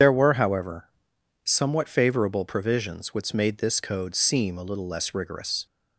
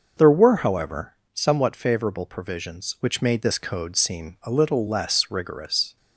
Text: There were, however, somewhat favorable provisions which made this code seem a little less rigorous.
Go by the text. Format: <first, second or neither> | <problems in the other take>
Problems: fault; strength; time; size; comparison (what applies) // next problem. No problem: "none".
second | loses the start of "There"; at 0.0 s; 50 ms // starts louder than the rest; strong; until 1.5 s; 7.5 dB